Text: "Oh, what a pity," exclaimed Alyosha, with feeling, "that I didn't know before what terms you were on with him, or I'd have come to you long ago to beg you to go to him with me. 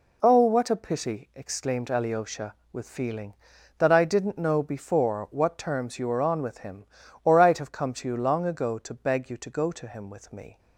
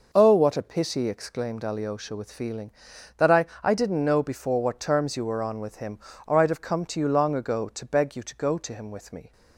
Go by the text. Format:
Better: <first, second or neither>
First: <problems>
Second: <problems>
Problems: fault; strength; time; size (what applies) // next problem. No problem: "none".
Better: first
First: none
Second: says "I" twice; at 3.6 s